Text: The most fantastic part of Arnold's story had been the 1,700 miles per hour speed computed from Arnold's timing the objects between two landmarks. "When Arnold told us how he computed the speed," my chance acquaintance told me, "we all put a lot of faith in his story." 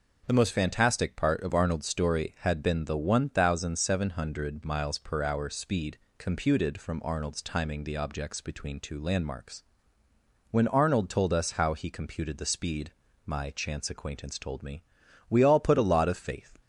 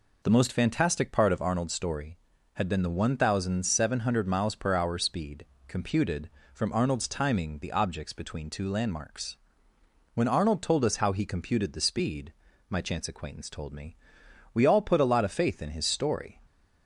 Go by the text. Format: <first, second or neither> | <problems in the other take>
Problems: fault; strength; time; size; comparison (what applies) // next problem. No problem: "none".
second | pauses between "speed" and "computed"; slight; at 5.9 s; 0.20 s long; slight in the second // stops before "in his story"; at 16.6 s